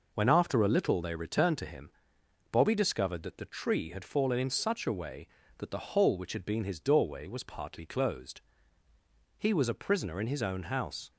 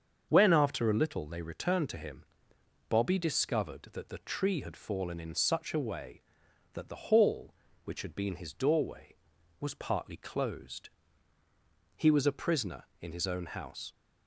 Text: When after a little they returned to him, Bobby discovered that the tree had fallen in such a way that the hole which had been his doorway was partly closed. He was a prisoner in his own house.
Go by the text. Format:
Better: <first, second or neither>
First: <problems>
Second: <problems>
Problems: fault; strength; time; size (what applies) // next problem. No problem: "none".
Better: first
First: none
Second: starts louder than the rest; until 1.3 s; 7 dB // says "hall" for "hole"; at 7.0 s